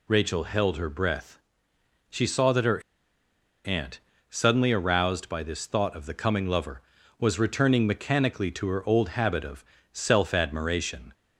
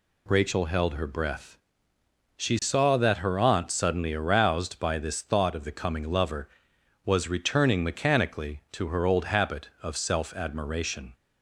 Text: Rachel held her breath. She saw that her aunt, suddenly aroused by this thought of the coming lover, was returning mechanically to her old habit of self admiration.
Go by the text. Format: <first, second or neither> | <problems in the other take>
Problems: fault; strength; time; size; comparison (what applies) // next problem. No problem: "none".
second | pauses between "her" and "aunt"; noticeable; at 2.8 s; 0.83 s long // pauses between "of" and "self"; slight; at 9.6 s; 0.28 s long